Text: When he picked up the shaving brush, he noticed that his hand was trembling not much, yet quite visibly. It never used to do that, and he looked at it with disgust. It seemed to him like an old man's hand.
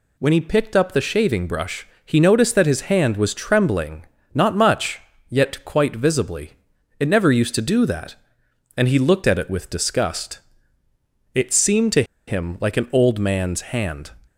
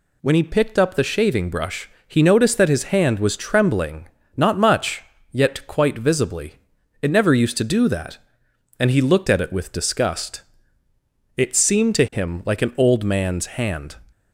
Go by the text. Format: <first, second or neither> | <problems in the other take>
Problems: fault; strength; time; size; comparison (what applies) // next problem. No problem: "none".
second | pauses between "trembling" and "not"; slight; at 4.0 s; 0.28 s long; slight in the second // pauses between "to" and "him"; slight; at 12.0 s; 0.24 s long